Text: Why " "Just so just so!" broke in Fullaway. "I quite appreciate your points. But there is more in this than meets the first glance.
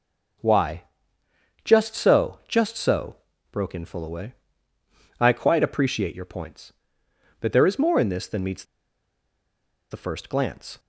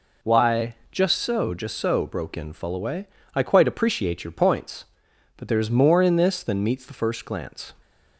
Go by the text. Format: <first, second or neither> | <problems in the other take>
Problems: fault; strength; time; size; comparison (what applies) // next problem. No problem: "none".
second | pauses between "meets" and "the"; strong; at 8.6 s; 1.2 s long